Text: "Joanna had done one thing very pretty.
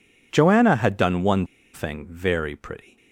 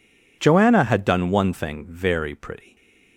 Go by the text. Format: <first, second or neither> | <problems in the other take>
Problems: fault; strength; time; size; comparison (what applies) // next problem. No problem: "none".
second | pauses between "one" and "thing"; slight; at 1.4 s; 0.28 s long